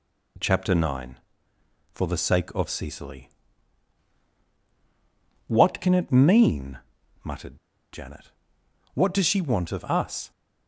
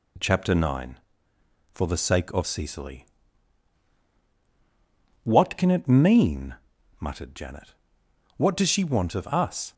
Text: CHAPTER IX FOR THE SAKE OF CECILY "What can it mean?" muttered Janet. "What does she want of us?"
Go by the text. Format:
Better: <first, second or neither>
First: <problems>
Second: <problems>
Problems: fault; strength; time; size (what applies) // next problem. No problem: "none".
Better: second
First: pauses between "CECILY" and "What"; strong; at 3.3 s; 2.1 s long // pauses between "muttered" and "Janet"; slight; at 7.5 s; 0.35 s long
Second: pauses between "CECILY" and "What"; strong; at 3.0 s; 2.1 s long